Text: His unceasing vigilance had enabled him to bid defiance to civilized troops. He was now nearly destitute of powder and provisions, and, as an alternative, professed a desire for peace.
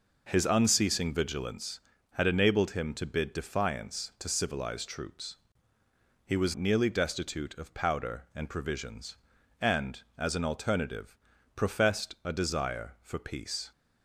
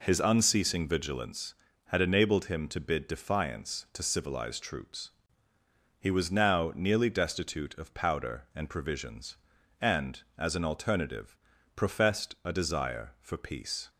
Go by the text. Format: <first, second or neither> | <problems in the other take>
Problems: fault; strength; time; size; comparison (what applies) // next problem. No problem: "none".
second | skips "now"; at 6.5 s